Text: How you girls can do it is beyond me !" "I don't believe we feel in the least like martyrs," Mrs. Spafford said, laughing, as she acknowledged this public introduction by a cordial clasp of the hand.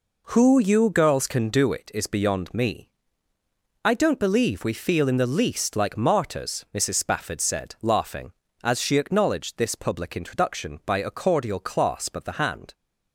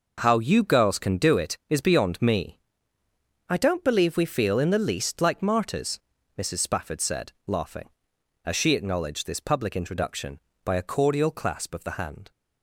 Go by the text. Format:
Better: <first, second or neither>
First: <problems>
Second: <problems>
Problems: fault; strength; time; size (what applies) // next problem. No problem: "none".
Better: second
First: says "Who" for "How"; at 0.2 s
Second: none